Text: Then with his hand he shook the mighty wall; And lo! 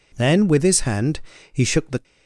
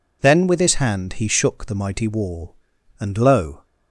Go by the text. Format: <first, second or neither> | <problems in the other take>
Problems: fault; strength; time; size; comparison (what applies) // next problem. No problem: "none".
second | pauses between "hand" and "he"; slight; at 1.2 s; 0.30 s long // stops before "mighty wall And lo"; at 2.0 s